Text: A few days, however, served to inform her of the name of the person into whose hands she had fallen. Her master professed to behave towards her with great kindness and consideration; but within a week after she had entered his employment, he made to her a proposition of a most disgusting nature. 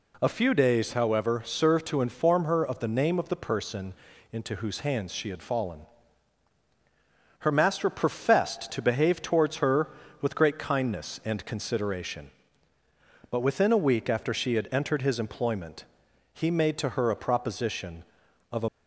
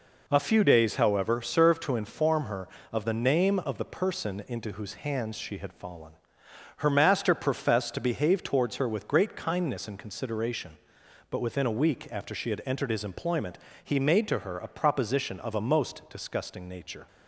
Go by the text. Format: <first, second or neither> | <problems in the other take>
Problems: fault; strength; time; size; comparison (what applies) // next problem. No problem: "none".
second | pauses between "person" and "into"; at 3.9 s; 0.38 s long // stops before "most disgusting nature"; at 18.6 s